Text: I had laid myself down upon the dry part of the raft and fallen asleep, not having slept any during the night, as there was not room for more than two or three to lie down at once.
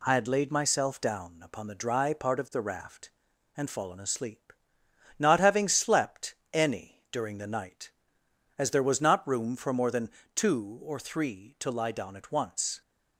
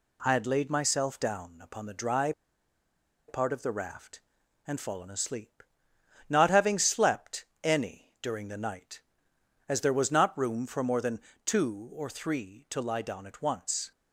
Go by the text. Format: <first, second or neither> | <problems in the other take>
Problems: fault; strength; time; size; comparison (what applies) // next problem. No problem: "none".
first | pauses between "dry" and "part"; noticeable; at 2.3 s; 0.97 s long // pauses between "slept" and "any"; slight; at 7.4 s; 0.18 s long; slight in the first // pauses between "than" and "two"; slight; at 11.2 s; 0.24 s long; slight in the first